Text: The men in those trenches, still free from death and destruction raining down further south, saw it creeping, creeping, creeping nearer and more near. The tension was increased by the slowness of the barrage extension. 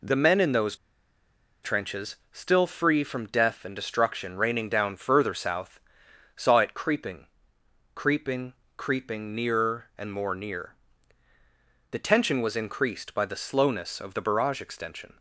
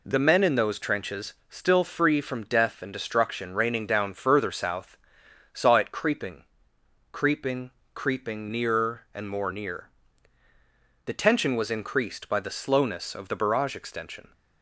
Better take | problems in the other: second | pauses between "those" and "trenches"; noticeable; at 0.7 s; 0.88 s long

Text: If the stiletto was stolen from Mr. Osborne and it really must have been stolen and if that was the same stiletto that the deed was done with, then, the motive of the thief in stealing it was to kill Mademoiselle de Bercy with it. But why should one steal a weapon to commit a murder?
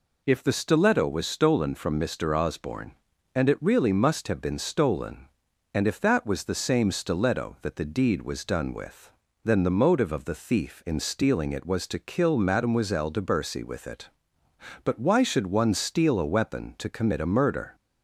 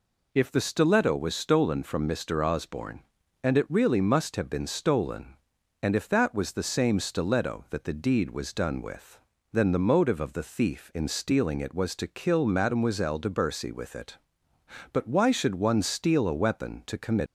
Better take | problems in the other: first | stops before "a murder"; at 17.2 s

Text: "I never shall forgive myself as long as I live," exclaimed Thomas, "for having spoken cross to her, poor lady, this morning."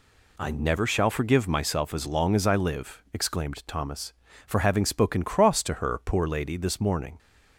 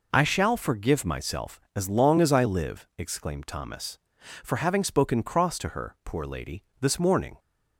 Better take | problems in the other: first | skips "never"; at 0.2 s

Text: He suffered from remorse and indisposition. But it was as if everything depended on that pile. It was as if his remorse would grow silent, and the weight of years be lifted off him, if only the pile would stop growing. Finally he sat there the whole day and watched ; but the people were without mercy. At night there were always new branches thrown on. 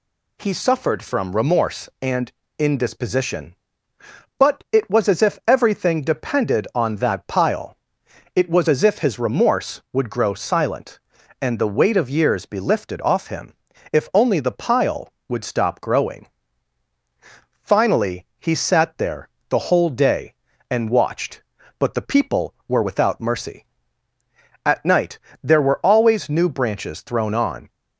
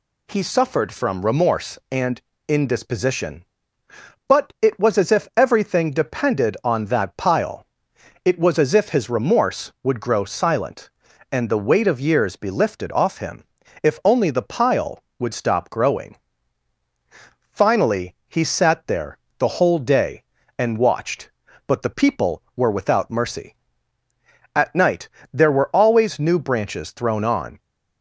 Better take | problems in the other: neither | pauses between "and" and "indisposition"; slight; the same in both // pauses between "there" and "the"; slight; the same in both // pauses between "night" and "there"; slight; the same in both

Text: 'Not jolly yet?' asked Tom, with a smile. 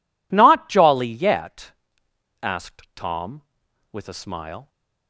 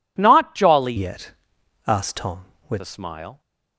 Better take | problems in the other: first | changes voice from "yet" to "with"; from 0.9 to 2.8 s; 1.9 s long

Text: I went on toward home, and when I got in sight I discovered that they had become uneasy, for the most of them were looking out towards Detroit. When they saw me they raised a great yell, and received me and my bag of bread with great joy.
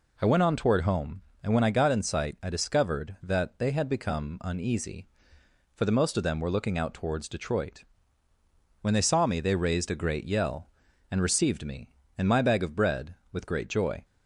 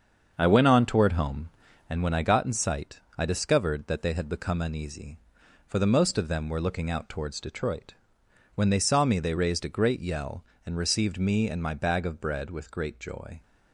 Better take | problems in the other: first | starts louder than the rest; until 1.9 s; 7 dB // pauses between "sight" and "I"; slight; at 2.9 s; 0.20 s long

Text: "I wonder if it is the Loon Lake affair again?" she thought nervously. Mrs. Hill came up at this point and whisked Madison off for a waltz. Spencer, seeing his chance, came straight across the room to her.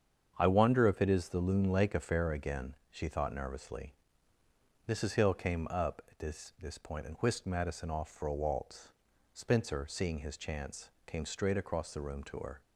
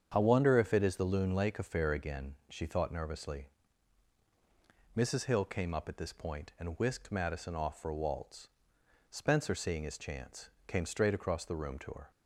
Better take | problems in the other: second | starts louder than the rest; strong; until 1.3 s; 7.5 dB; strong in the second // says "this" twice; at 6.5 s

